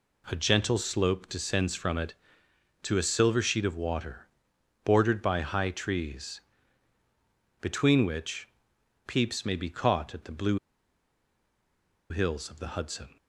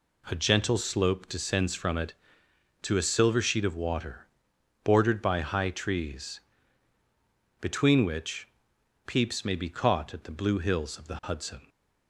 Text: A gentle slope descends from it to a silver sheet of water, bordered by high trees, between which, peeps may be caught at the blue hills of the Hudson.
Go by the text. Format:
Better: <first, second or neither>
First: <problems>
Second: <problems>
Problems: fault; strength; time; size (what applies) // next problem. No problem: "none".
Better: second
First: pauses between "blue" and "hills"; strong; at 10.5 s; 1.5 s long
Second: none